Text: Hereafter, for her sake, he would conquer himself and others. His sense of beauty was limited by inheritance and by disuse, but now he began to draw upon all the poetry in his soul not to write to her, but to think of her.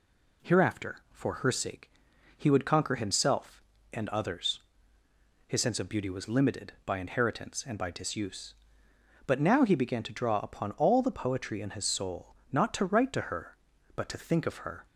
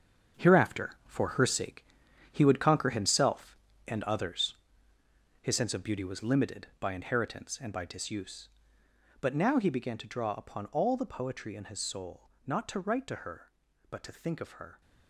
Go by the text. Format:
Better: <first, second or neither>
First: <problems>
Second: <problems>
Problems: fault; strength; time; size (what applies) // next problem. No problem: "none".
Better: first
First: pauses between "soul" and "not"; slight; at 12.3 s; 0.18 s long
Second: gets quieter; strong; throughout; 10 dB // pauses between "soul" and "not"; slight; at 12.2 s; 0.18 s long